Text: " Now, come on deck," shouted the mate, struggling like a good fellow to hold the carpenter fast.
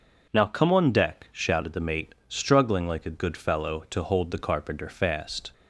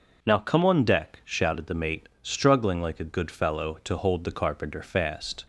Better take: neither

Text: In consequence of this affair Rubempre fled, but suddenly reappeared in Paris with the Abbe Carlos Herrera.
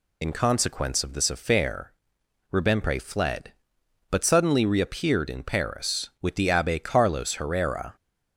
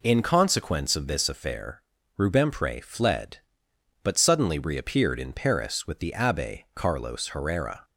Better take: second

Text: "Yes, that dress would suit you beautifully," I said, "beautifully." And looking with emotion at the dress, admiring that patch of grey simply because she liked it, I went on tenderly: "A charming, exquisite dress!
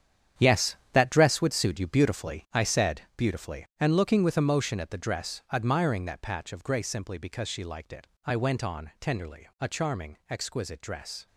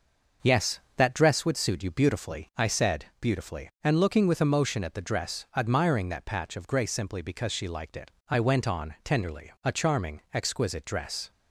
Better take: second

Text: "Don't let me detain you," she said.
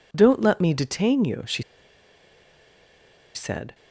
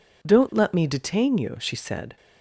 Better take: second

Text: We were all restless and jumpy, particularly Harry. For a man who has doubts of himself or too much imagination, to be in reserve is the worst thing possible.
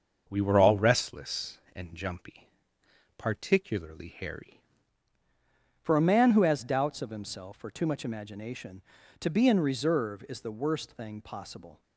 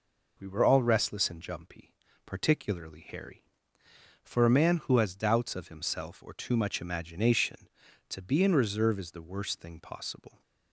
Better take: second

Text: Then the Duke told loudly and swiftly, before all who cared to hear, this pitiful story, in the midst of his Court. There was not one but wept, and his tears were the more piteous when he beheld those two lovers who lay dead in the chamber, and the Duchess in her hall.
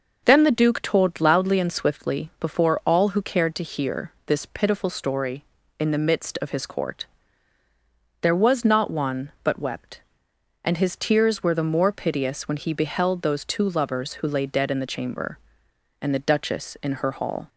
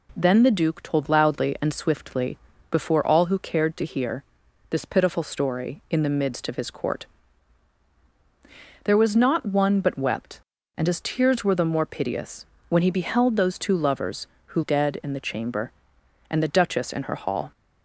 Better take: first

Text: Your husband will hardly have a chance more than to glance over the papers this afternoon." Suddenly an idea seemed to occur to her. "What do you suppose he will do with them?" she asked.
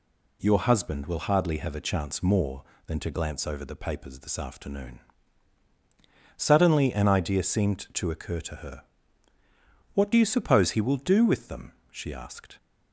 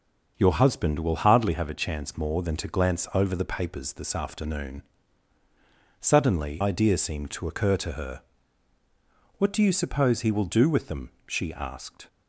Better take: first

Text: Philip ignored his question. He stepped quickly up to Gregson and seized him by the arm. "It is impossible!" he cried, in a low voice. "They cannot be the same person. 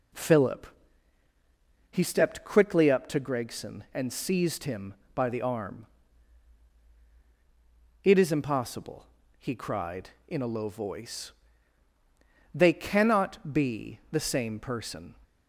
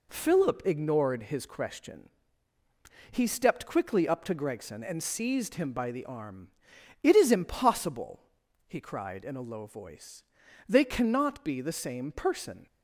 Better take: second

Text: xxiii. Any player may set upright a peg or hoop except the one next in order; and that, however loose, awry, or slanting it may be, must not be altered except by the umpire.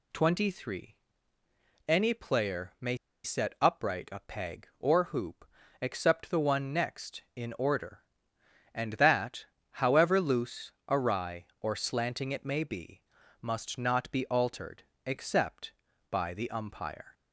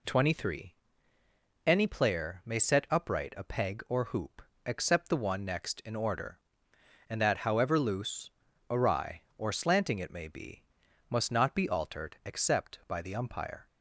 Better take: second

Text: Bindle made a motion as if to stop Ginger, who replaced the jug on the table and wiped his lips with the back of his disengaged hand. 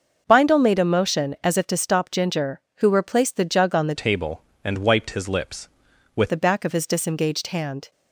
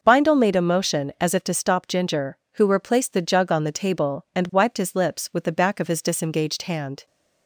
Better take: second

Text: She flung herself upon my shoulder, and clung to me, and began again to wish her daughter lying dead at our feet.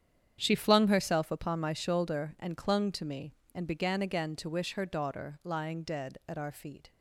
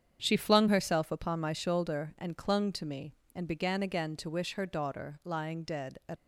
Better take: first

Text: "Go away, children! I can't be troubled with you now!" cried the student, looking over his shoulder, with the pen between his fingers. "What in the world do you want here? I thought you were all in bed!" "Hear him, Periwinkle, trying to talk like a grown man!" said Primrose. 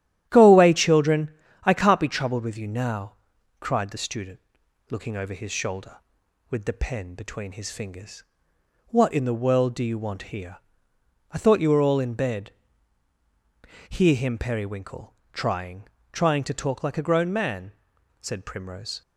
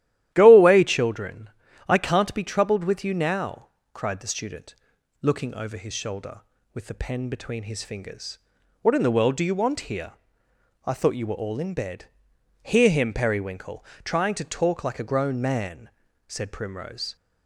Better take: second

